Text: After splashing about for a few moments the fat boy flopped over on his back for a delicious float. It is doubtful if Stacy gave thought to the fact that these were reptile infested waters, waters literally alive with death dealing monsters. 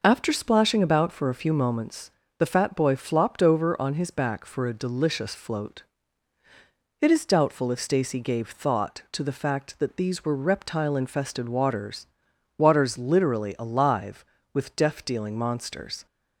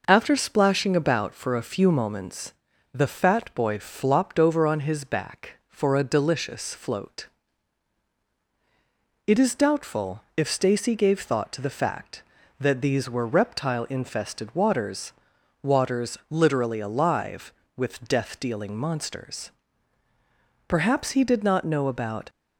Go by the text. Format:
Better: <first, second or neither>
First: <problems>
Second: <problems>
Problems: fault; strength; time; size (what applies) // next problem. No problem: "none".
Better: first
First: pauses between "moments" and "the"; slight; at 2.0 s; 0.30 s long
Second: pauses between "moments" and "the"; at 2.5 s; 0.40 s long // pauses between "doubtful" and "if"; slight; at 10.2 s; 0.16 s long // goes on to say "Perhaps he did not know about"; from 20.6 s on; 1.6 s long